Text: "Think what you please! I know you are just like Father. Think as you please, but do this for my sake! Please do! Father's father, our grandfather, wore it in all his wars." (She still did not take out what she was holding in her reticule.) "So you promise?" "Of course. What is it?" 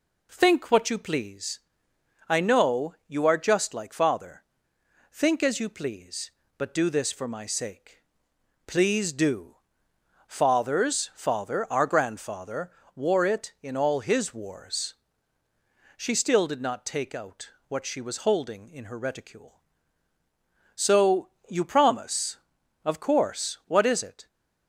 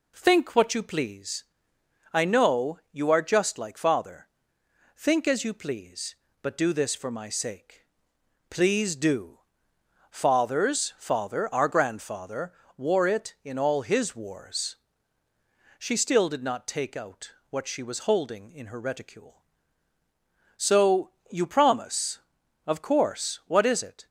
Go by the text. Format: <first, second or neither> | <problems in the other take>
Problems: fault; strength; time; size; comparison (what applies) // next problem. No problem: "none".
neither | pauses between "out" and "what"; slight; the same in both // pauses between "So" and "you"; slight; the same in both